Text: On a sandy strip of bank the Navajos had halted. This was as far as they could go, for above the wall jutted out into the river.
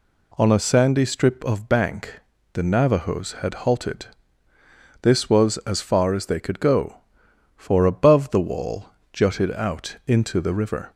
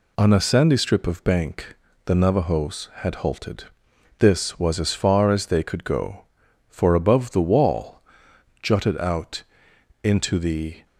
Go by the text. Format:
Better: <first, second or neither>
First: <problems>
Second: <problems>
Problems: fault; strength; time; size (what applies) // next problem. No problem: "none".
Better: first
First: pauses between "bank" and "the"; slight; at 2.2 s; 0.34 s long // pauses between "wall" and "jutted"; slight; at 8.8 s; 0.26 s long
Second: pauses between "bank" and "the"; slight; at 1.7 s; 0.30 s long // pauses between "wall" and "jutted"; noticeable; at 7.9 s; 0.62 s long // pauses between "out" and "into"; noticeable; at 9.4 s; 0.60 s long // stops before "river"; at 10.8 s